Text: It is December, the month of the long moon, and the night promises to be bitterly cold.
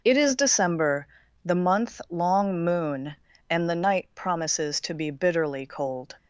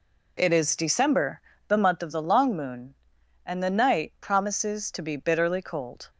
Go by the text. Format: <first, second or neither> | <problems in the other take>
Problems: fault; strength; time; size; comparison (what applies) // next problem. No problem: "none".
second | skips "of the"; at 2.0 s